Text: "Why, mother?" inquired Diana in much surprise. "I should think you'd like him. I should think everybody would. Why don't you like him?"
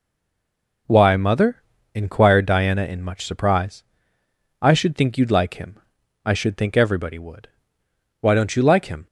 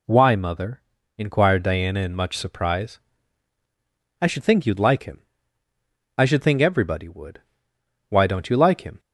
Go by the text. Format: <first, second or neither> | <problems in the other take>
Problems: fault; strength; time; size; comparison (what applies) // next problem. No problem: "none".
second | stays silent before the first word; slight; until 0.8 s; 0.8 s long